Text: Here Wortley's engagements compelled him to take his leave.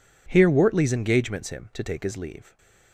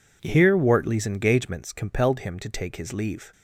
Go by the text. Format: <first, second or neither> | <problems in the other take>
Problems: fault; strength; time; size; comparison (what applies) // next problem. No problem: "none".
second | skips "compelled"; at 1.4 s // stays silent after the last word; slight; from 2.4 s on; 0.5 s long